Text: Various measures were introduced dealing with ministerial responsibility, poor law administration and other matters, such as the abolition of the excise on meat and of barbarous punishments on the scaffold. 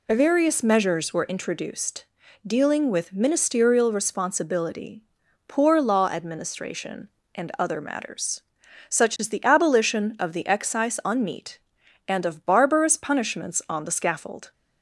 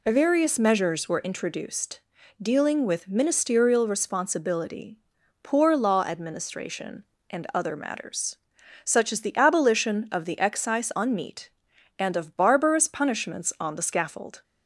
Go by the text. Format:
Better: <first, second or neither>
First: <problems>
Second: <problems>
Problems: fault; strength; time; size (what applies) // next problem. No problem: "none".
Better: neither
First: pauses between "introduced" and "dealing"; at 2.0 s; 0.40 s long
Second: pauses between "introduced" and "dealing"; at 2.0 s; 0.40 s long